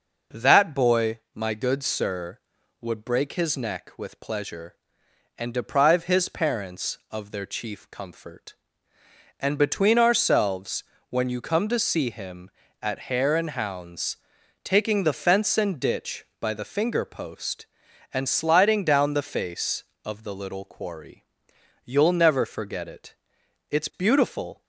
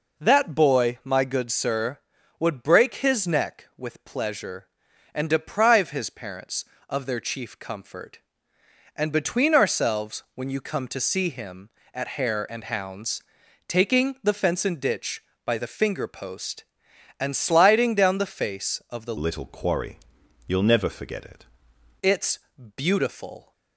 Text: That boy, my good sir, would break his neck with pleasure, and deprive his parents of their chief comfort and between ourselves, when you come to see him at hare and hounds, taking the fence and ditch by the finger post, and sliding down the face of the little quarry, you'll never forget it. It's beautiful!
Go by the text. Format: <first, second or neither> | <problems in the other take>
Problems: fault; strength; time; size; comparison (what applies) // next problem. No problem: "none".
first | changes voice from "little" to "it"; from 19.1 to 21.4 s; 2.3 s long // pauses between "It's" and "beautiful"; at 22.3 s; 0.38 s long